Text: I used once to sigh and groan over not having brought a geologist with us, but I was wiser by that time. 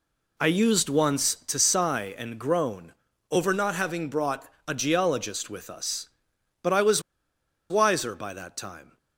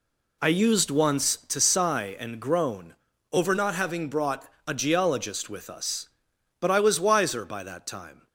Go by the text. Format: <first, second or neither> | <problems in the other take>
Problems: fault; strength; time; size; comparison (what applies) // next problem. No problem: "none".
second | pauses between "groan" and "over"; at 2.9 s; 0.38 s long; also in the second // pauses between "brought" and "a"; slight; at 4.4 s; 0.20 s long; slight in the second // pauses between "was" and "wiser"; noticeable; at 7.0 s; 0.69 s long